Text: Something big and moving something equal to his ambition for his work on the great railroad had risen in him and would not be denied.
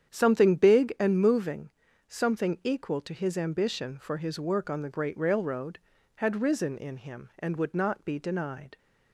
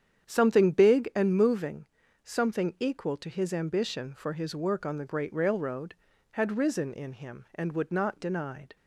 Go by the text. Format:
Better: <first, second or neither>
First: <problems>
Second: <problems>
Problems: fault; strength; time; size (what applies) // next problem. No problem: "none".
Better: first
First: starts louder than the rest; strong; until 1.1 s; 9 dB // pauses between "moving" and "something"; at 1.6 s; 0.42 s long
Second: starts louder than the rest; strong; until 1.3 s; 8.5 dB // pauses between "moving" and "something"; at 1.8 s; 0.42 s long // skips "be"; at 8.1 s